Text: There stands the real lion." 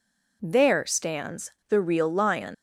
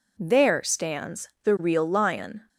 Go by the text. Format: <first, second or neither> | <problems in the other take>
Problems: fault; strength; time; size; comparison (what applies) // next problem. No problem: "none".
second | pauses between "stands" and "the"; slight; at 1.5 s; 0.16 s long // leaves "lion" unfinished; at 2.5 s; 170 ms